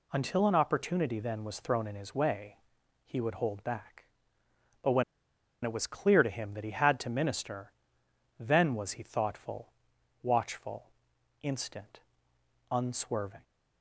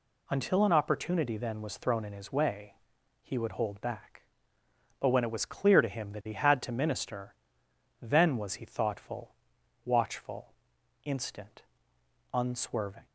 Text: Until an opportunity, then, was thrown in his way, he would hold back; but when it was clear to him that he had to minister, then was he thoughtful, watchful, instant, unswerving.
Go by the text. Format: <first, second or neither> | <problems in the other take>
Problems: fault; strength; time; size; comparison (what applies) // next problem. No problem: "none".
second | pauses between "when" and "it"; noticeable; at 5.0 s; 0.59 s long